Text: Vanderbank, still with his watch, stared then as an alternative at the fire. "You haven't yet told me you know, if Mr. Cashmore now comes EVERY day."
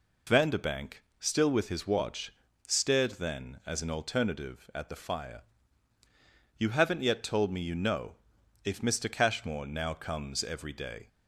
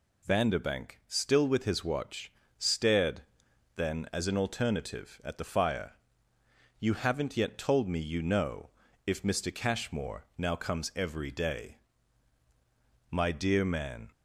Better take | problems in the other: first | pauses between "stared" and "then"; noticeable; at 3.2 s; 0.54 s long // goes on to say "My dear man"; noticeable; from 13.1 s on; 1.0 s long

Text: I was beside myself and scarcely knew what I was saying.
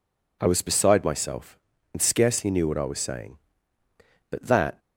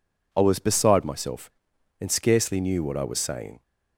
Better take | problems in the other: second | goes on to say "But that"; slight; from 4.3 s on; 0.48 s long

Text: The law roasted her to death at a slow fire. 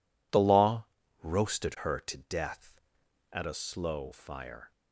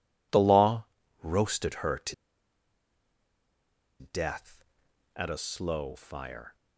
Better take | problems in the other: first | pauses between "law" and "roasted"; slight; at 0.8 s; 0.34 s long; slight in the first // pauses between "to" and "death"; strong; at 2.1 s; 1.8 s long

